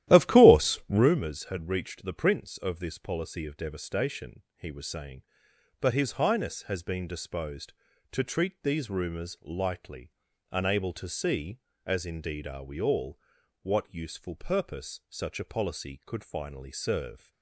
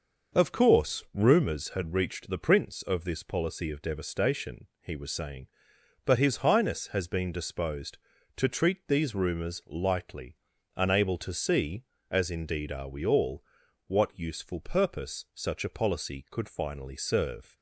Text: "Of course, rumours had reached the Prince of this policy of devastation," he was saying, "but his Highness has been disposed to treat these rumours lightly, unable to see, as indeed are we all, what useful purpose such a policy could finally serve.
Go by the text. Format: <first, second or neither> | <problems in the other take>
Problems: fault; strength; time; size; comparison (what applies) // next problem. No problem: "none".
second | starts louder than the rest; strong; until 1.1 s; 13 dB